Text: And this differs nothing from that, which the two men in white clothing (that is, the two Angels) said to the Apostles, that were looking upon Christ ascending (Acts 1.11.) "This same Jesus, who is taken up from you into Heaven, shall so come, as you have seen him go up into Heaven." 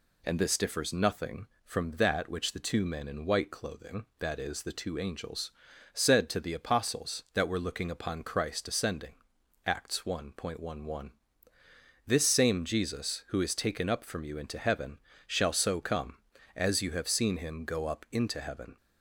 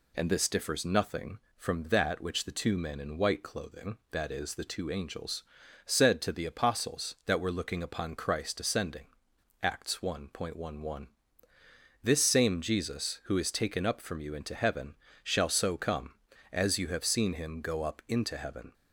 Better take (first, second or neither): neither